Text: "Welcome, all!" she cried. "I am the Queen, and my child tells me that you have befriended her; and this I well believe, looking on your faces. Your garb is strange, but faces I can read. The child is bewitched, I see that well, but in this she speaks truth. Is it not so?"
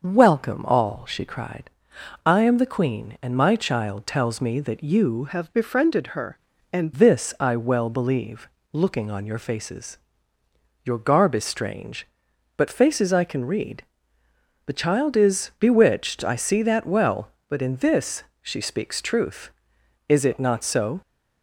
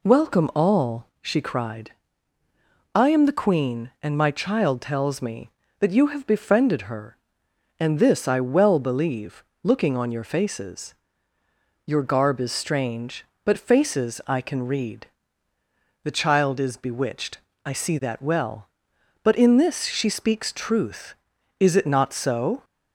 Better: second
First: starts louder than the rest; noticeable; until 1.0 s; 6 dB // changes voice from "have" to "and"; from 5.2 to 6.9 s; 1.7 s long // pauses between "this" and "she"; slight; at 18.2 s; 0.18 s long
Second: none

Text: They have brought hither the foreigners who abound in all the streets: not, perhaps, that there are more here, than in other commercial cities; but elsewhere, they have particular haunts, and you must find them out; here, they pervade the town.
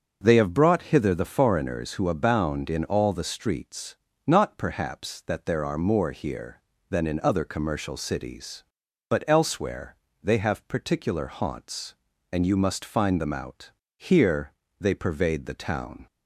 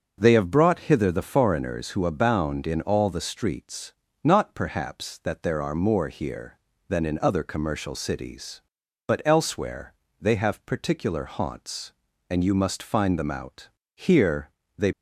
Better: first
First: starts louder than the rest; until 1.2 s; 6.5 dB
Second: starts louder than the rest; until 1.2 s; 6.5 dB // stops before "pervade the town"; at 14.9 s

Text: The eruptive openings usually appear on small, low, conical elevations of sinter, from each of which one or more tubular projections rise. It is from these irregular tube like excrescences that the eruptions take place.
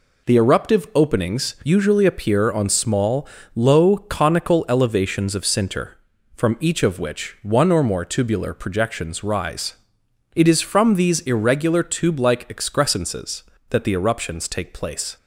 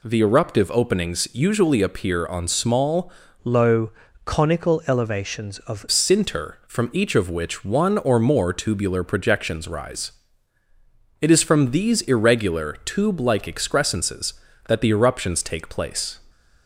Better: first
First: none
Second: changes voice from "low" to "of"; from 3.4 to 5.8 s; 2.4 s long

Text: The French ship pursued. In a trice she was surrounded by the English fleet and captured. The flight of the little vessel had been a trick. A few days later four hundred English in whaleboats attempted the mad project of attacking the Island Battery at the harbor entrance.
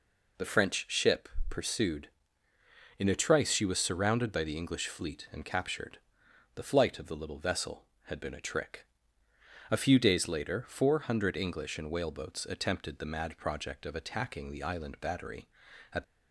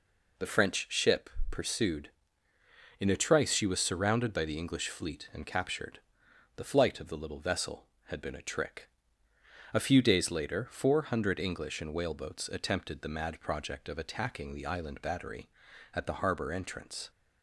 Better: second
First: pauses between "ship" and "pursued"; slight; at 1.2 s; 0.20 s long // stops before "the harbor entrance"; at 16.0 s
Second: pauses between "ship" and "pursued"; slight; at 1.3 s; 0.20 s long

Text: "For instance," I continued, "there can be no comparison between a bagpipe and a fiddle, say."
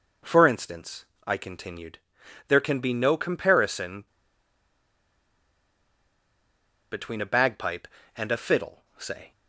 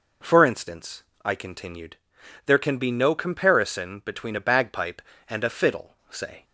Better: second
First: pauses between "comparison" and "between"; strong; at 4.0 s; 2.8 s long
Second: none

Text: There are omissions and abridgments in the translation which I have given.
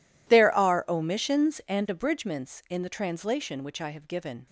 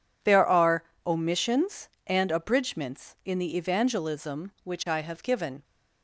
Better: first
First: none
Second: pauses between "are" and "omissions"; slight; at 0.8 s; 0.24 s long // says "evangelism" for "translation"; at 3.5 s

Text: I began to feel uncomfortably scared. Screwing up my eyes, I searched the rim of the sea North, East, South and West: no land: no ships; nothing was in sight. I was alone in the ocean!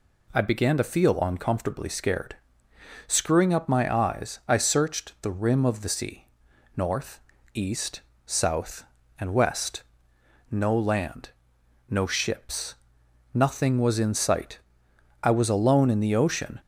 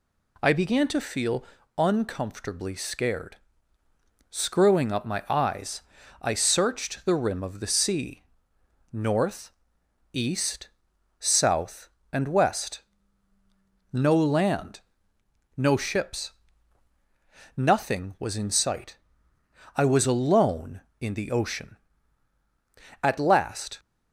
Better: first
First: pauses between "sea" and "North"; noticeable; at 6.2 s; 0.48 s long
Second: pauses between "feel" and "uncomfortably"; slight; at 1.4 s; 0.34 s long // pauses between "sea" and "North"; noticeable; at 8.2 s; 0.70 s long // goes on to say "At last"; noticeable; from 23.0 s on; 0.78 s long

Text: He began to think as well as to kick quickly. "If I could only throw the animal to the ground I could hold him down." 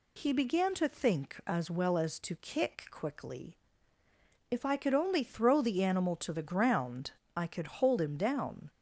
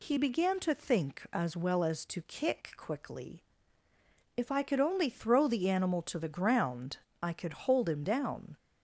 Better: neither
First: pauses between "ground" and "I"; slight; at 7.1 s; 0.24 s long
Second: pauses between "ground" and "I"; slight; at 6.9 s; 0.24 s long

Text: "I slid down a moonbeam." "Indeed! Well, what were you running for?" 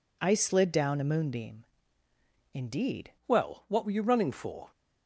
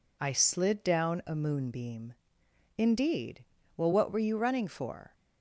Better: second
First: changes voice at "Well"; from 3.2 s on; 1.5 s long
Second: none

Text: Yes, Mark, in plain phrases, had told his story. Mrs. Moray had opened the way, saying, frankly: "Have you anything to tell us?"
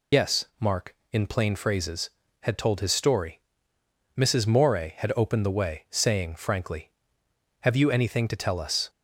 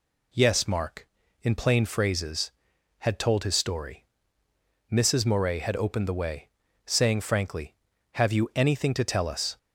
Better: second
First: loses the start of "Yes"; at 0.1 s; 90 ms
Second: none

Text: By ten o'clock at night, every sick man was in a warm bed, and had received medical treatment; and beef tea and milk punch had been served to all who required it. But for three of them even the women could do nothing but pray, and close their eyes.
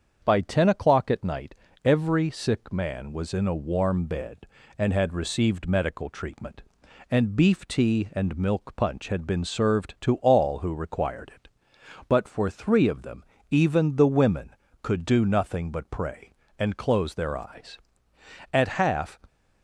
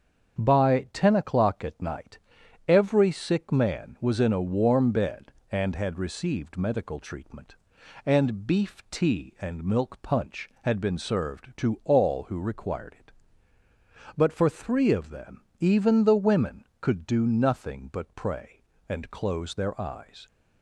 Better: second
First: starts louder than the rest; strong; until 1.2 s; 7.5 dB // pauses between "them" and "even"; slight; at 13.2 s; 0.26 s long // goes on to say "At half"; noticeable; from 18.5 s on; 0.66 s long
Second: starts louder than the rest; strong; until 1.4 s; 7.5 dB // pauses between "them" and "even"; slight; at 15.4 s; 0.18 s long

